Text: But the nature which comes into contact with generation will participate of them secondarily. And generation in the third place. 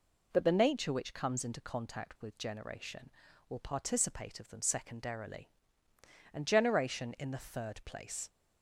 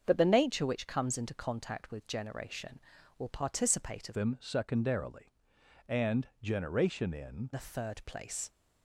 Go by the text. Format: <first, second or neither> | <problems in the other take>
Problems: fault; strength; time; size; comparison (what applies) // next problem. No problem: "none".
first | starts louder than the rest; until 1.0 s; 7 dB // changes voice from "them" to "in"; from 4.1 to 7.4 s; 3.3 s long